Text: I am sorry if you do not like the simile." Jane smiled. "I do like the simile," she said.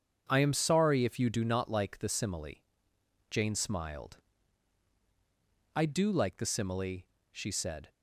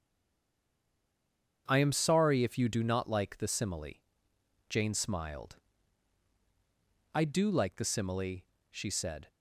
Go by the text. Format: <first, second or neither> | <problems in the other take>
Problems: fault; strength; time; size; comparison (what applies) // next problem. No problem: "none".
first | stays silent before the first word; noticeable; until 1.6 s; 1.6 s long // starts louder than the rest; until 2.6 s; 7 dB; also in the first